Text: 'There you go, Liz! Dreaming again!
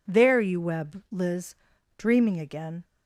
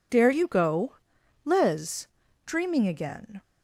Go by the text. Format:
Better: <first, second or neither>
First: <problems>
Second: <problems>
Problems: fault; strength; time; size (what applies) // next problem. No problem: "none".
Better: second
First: says "web" for "go"; at 0.6 s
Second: none